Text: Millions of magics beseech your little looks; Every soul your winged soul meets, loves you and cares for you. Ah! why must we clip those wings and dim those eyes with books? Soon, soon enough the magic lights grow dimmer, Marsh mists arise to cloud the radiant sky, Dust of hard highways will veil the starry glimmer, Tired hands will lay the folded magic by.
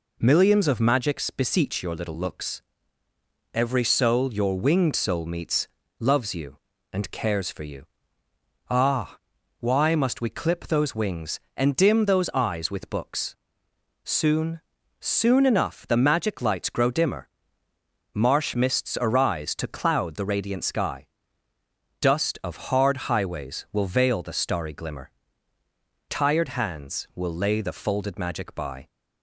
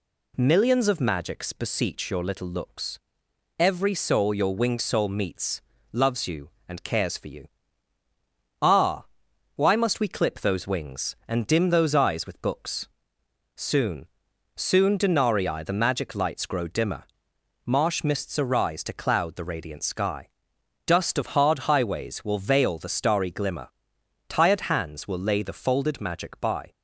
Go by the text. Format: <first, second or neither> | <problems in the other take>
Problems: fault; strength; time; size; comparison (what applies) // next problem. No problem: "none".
first | says "denarii" for "enough"; at 14.9 s